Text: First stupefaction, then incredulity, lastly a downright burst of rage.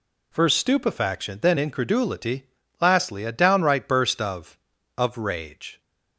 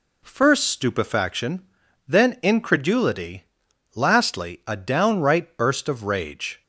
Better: second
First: says "of" twice; at 4.9 s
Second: none

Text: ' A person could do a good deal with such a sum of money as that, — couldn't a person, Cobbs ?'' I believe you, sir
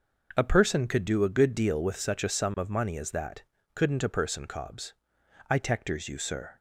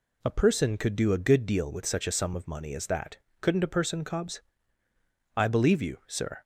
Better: second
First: starts louder than the rest; noticeable; until 1.3 s; 6 dB // says "tectors" for "believe"; at 5.5 s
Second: none

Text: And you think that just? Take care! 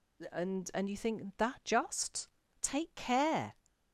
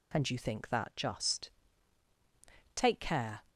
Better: second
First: says "And" twice; at 0.7 s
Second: none

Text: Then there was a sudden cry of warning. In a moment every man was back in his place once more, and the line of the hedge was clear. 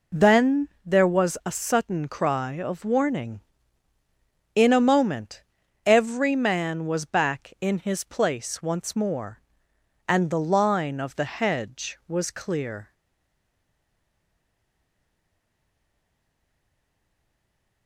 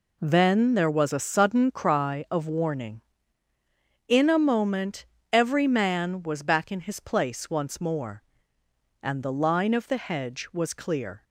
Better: second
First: pauses between "Then" and "there"; slight; at 0.6 s; 0.18 s long // pauses between "moment" and "every"; noticeable; at 5.4 s; 0.46 s long // stays silent after the last word; strong; from 12.9 s on; 4.9 s long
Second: pauses between "moment" and "every"; slight; at 5.0 s; 0.26 s long

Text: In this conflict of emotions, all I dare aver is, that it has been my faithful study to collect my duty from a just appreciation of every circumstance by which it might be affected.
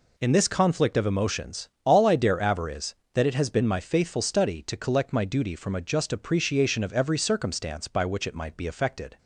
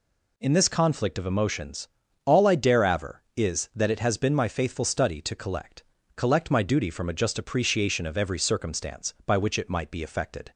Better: first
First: none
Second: says "collect" twice; at 6.1 s

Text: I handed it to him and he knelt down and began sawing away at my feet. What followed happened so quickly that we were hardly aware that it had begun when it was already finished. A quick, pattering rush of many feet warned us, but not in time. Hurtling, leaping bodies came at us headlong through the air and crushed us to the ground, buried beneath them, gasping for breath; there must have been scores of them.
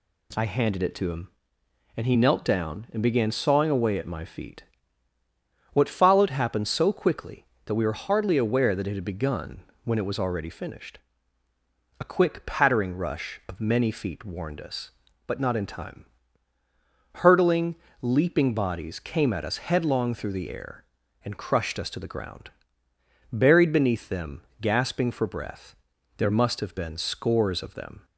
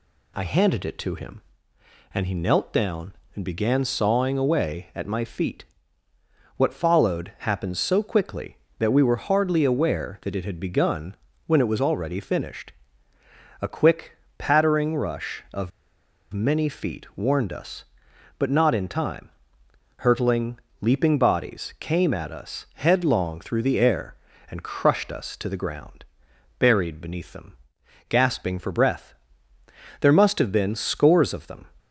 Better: first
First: pauses between "begun" and "when"; slight; at 9.6 s; 0.20 s long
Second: pauses between "begun" and "when"; slight; at 11.1 s; 0.32 s long // pauses between "of" and "many"; noticeable; at 15.7 s; 0.63 s long

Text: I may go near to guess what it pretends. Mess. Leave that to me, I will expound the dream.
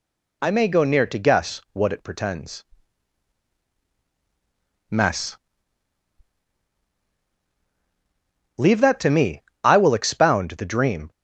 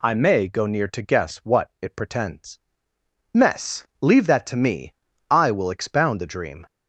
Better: neither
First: none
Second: none

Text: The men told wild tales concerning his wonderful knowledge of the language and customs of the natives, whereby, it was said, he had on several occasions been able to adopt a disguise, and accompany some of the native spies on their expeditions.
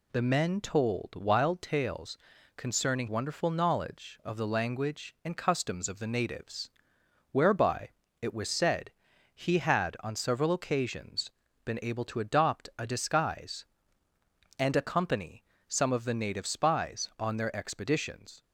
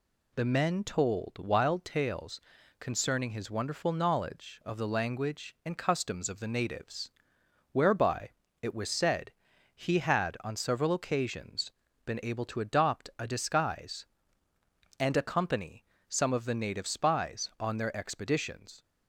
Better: second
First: pauses between "tales" and "concerning"; at 2.1 s; 0.38 s long // skips "his"; at 3.0 s // pauses between "occasions" and "been"; slight; at 11.3 s; 0.34 s long // pauses between "accompany" and "some"; slight; at 15.4 s; 0.24 s long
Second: pauses between "tales" and "concerning"; at 2.4 s; 0.38 s long // pauses between "occasions" and "been"; slight; at 11.7 s; 0.34 s long // pauses between "accompany" and "some"; slight; at 15.8 s; 0.24 s long

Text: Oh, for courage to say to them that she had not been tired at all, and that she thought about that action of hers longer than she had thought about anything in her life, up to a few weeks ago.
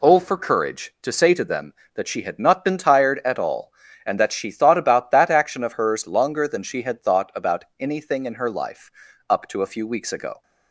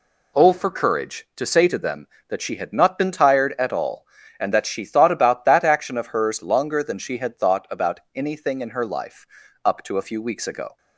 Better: neither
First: pauses between "about" and "anything"; slight; at 7.6 s; 0.16 s long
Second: pauses between "about" and "anything"; slight; at 7.9 s; 0.16 s long

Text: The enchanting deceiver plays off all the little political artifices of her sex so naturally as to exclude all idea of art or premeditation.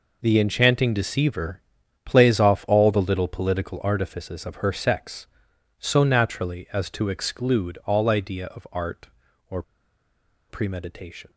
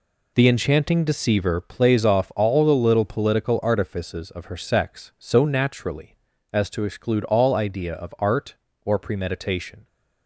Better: second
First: pauses between "deceiver" and "plays"; at 1.6 s; 0.44 s long // pauses between "or" and "premeditation"; noticeable; at 9.6 s; 0.85 s long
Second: none

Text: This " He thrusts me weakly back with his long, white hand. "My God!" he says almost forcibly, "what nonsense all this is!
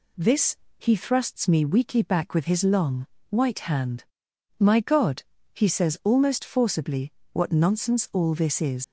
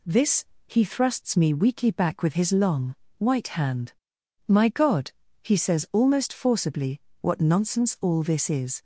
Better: second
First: leaves "is" unfinished; at 8.8 s; 90 ms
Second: none

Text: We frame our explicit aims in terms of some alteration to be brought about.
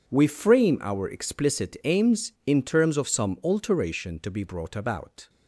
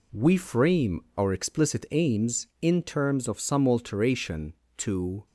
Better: first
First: none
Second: pauses between "frame" and "our"; slight; at 1.0 s; 0.16 s long // stops before "be brought about"; at 5.2 s

